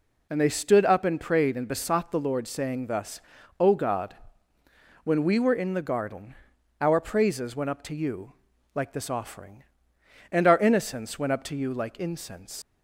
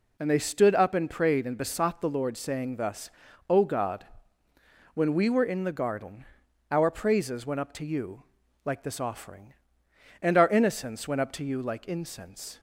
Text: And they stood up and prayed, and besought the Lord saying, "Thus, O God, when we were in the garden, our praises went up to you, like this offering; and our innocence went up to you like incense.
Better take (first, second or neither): second